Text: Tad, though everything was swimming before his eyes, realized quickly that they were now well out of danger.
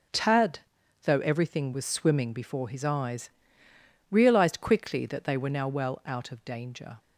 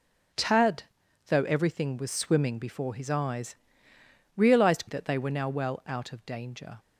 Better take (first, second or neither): first